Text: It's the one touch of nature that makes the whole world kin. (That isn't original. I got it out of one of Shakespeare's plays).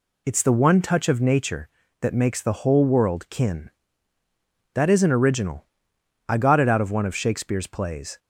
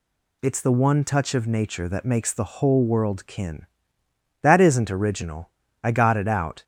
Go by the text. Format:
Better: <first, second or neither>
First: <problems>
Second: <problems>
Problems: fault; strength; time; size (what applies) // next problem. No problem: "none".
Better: first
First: none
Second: stops before "of one of Shakespeare's plays"; at 6.6 s